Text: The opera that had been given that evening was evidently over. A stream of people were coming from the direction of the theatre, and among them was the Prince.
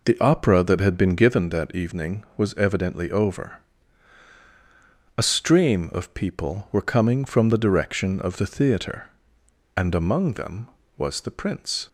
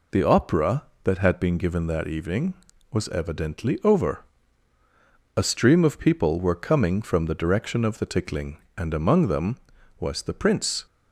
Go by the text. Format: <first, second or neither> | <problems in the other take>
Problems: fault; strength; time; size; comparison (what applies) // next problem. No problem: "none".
first | says "tickling" for "theatre"; at 8.0 s